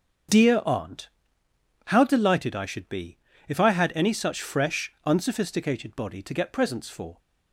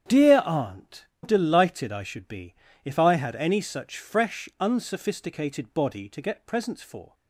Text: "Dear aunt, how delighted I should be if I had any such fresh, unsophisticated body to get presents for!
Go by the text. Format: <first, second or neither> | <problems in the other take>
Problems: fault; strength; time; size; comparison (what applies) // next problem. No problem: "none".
first | starts louder than the rest; strong; until 1.3 s; 8.5 dB; also in the first // skips "how"; at 1.1 s // pauses between "be" and "if"; slight; at 2.5 s; 0.30 s long; slight in the first